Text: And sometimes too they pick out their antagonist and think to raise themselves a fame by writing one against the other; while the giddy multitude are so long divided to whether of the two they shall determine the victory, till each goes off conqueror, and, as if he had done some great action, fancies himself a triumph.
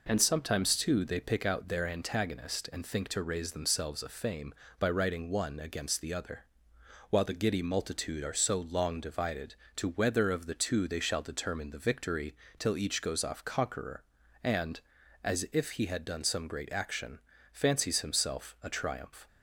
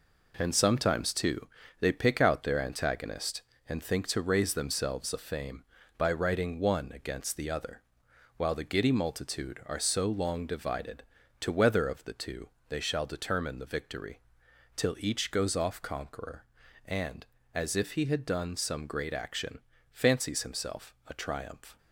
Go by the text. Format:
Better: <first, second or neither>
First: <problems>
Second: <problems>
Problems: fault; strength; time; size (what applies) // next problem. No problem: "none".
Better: first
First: none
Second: gets quieter; throughout; 6.5 dB // pauses between "too" and "they"; slight; at 1.4 s; 0.32 s long // pauses between "two" and "they"; slight; at 12.4 s; 0.18 s long